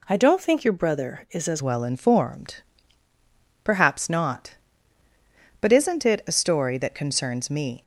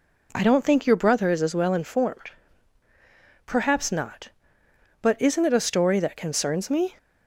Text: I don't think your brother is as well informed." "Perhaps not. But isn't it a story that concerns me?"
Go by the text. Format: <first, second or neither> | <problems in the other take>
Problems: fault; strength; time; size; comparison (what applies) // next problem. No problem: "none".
second | changes voice at "well"; from 1.6 s on; 6.2 s long